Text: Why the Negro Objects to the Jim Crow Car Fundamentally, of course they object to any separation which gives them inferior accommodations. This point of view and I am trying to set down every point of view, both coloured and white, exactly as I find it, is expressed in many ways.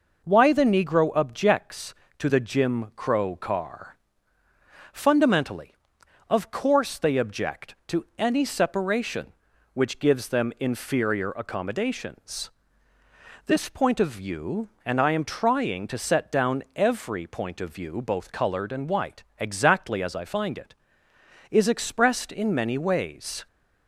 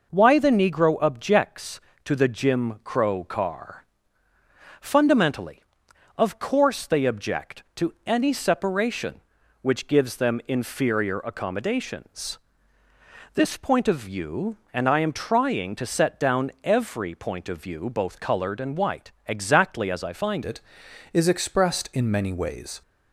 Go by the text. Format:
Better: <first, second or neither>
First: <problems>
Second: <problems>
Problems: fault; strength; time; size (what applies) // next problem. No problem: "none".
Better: first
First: pauses between "Car" and "Fundamentally"; noticeable; at 3.9 s; 0.96 s long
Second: pauses between "Car" and "Fundamentally"; noticeable; at 3.8 s; 0.96 s long // changes voice at "it"; from 20.4 s on; 2.4 s long